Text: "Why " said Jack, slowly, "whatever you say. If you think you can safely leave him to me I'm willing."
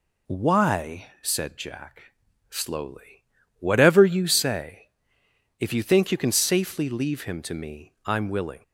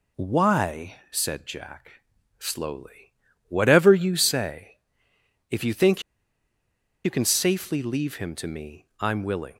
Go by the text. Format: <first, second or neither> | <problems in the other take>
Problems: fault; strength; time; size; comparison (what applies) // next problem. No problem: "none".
first | pauses between "think" and "you"; at 6.0 s; 1.0 s long // pauses between "me" and "I'm"; slight; at 8.8 s; 0.16 s long